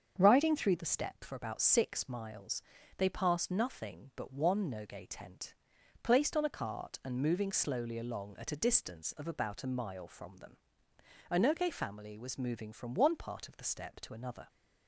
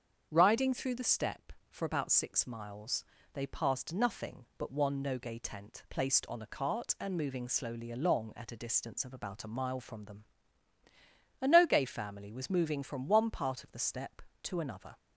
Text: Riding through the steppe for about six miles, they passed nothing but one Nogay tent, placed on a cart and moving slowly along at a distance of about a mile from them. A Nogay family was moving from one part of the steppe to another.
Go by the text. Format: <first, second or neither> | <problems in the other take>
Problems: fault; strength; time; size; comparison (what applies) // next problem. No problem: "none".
neither | starts louder than the rest; strong; the same in both